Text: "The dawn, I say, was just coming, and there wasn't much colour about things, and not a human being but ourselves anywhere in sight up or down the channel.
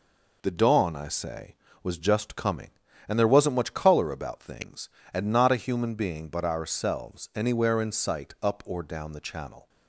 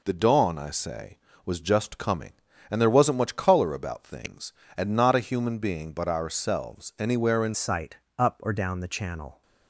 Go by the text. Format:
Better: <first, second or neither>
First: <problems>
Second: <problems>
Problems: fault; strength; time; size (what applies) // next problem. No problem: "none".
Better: first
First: none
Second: changes voice at "sight"; from 7.5 s on; 1.9 s long // pauses between "sight" and "up"; slight; at 7.9 s; 0.20 s long